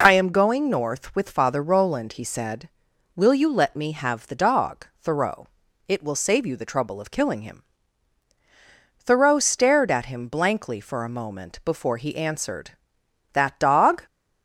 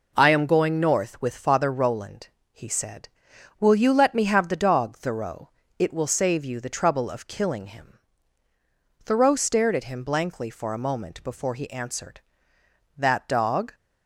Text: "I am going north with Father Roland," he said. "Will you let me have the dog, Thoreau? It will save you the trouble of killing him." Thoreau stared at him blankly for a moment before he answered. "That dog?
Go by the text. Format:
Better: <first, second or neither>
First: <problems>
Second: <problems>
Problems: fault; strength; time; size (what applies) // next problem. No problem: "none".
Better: neither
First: none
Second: none